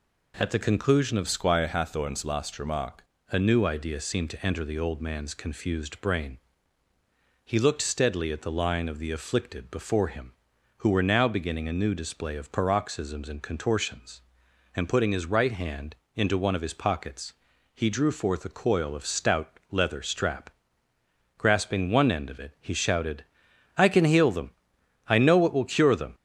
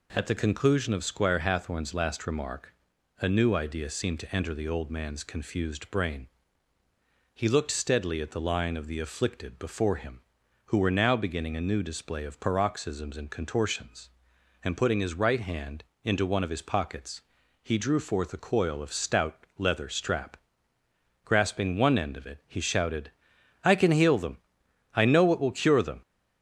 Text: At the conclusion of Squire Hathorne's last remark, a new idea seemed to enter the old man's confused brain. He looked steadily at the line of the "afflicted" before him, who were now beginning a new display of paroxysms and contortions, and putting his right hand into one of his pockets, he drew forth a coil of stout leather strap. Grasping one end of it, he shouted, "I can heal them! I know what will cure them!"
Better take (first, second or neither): second